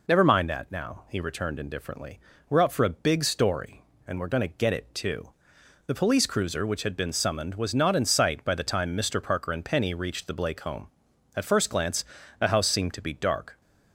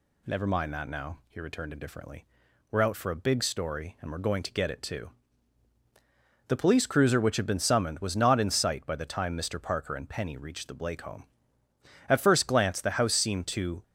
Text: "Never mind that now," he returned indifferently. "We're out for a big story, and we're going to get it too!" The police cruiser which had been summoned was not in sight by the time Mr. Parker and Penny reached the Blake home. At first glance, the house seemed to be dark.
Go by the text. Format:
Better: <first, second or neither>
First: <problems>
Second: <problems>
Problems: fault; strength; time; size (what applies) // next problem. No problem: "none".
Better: first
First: none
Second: stops before "be dark"; at 13.8 s